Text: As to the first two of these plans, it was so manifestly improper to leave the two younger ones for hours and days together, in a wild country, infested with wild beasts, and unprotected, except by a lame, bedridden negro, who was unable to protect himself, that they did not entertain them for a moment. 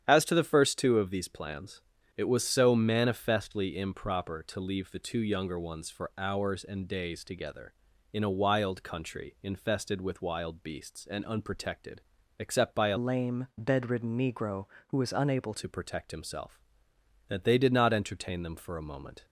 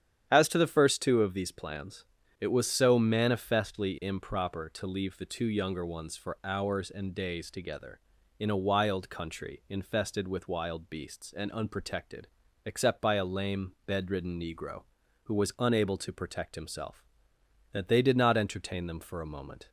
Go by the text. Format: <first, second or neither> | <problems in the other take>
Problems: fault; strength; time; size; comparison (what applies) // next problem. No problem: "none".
second | starts louder than the rest; strong; until 1.0 s; 9.5 dB; strong in the second // changes voice from "lame" to "unable"; from 12.9 to 15.5 s; 2.6 s long